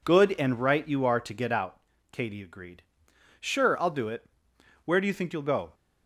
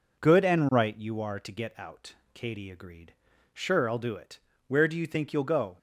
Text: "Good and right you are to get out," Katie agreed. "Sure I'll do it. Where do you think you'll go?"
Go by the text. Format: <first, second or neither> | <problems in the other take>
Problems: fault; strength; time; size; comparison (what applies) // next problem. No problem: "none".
neither | none